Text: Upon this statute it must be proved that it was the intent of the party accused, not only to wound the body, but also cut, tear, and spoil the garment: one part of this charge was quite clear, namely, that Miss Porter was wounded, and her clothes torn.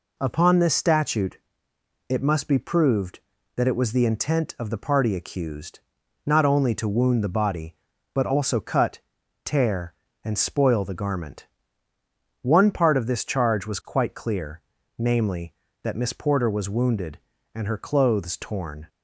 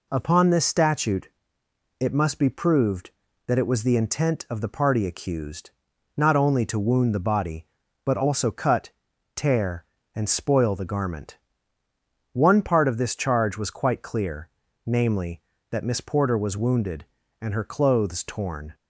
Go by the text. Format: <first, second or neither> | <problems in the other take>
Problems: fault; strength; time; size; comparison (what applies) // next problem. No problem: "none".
neither | pauses between "statute" and "it"; noticeable; the same in both